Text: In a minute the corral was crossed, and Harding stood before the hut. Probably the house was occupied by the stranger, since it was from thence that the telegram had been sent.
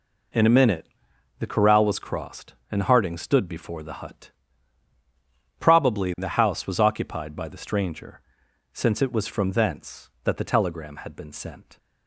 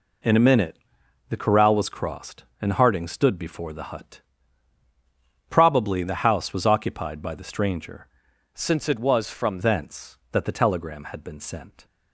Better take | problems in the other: first | pauses between "minute" and "the"; noticeable; at 0.7 s; 0.52 s long; noticeable in the first // changes voice from "since" to "from"; from 8.5 to 9.5 s; 1.0 s long

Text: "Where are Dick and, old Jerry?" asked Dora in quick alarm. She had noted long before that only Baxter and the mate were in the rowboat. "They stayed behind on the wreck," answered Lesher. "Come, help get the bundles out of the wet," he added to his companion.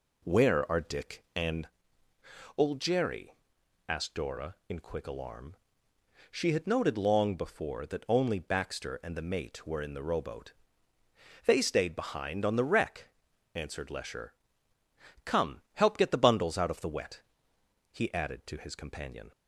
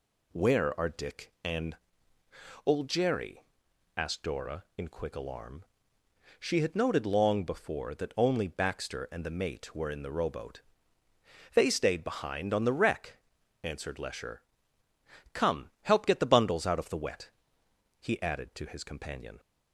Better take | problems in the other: second | starts louder than the rest; slight; until 1.6 s; 3 dB

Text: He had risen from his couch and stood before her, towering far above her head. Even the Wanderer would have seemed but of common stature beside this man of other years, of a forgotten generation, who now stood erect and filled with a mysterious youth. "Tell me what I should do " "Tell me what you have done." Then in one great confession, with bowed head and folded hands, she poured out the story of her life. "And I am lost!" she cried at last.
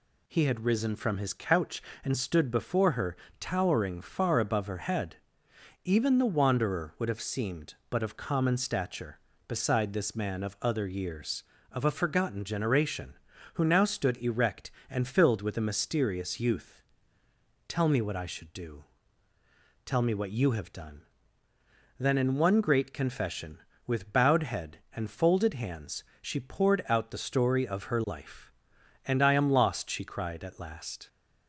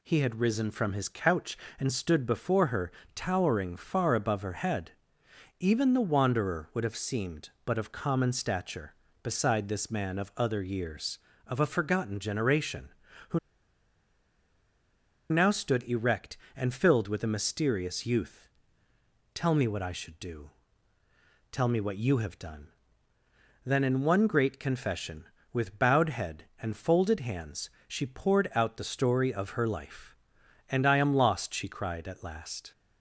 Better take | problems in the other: first | pauses between "who" and "now"; strong; at 13.3 s; 1.9 s long

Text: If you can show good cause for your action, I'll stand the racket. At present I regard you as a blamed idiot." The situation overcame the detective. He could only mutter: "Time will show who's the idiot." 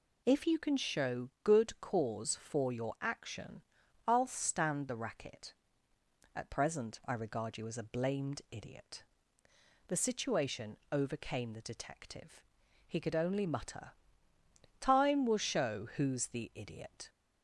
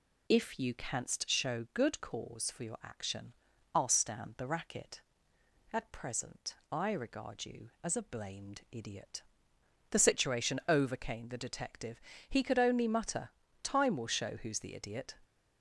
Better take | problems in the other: first | says "canst" for "can"; at 0.7 s // pauses between "present" and "I"; slight; at 6.5 s; 0.18 s long

